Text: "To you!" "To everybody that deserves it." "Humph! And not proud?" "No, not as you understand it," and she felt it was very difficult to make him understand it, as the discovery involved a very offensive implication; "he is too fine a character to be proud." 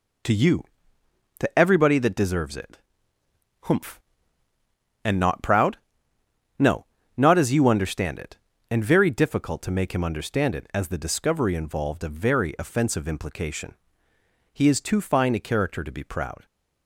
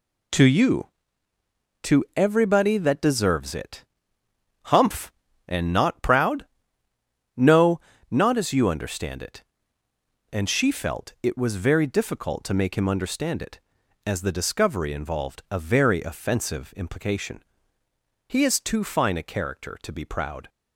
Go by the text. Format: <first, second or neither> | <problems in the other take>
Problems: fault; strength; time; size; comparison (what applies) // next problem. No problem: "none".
second | skips "she felt it was"; at 8.8 s